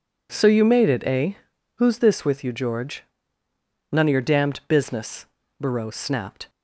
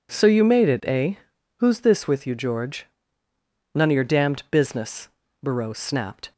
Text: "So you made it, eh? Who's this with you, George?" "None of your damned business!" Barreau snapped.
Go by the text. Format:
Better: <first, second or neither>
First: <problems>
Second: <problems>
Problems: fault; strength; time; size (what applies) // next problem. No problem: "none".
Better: neither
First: none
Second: none